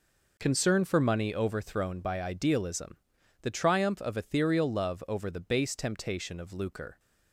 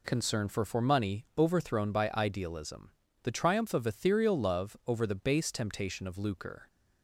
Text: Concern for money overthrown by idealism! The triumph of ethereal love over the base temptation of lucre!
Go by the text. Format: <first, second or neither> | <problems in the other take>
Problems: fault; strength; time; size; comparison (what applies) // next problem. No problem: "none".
first | says "for" twice; at 0.6 s